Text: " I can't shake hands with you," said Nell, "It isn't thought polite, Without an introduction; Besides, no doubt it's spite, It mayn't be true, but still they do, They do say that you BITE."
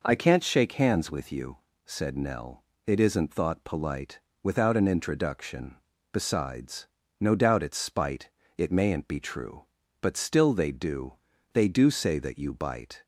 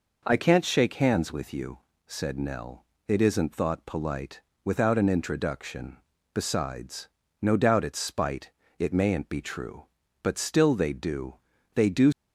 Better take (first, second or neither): first